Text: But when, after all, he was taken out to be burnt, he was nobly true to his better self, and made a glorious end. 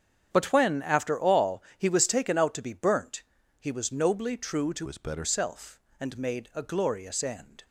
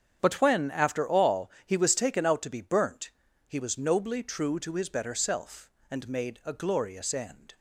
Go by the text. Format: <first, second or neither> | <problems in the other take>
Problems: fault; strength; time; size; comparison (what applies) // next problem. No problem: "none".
second | starts louder than the rest; strong; until 1.3 s; 8.5 dB; strong in the second // changes voice from "his" to "better"; from 4.8 to 5.2 s; 0.4 s long